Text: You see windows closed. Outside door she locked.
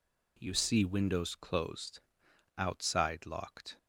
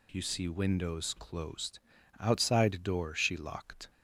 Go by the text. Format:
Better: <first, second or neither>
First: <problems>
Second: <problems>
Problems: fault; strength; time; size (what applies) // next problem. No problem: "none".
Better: second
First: skips "door she"; at 3.2 s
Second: none